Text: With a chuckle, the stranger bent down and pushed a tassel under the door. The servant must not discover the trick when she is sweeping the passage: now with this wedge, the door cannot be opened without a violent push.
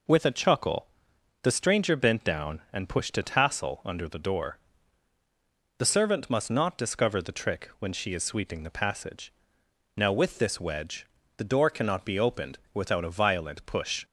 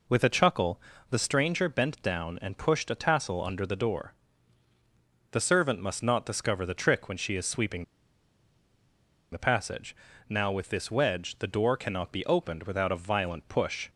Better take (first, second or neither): first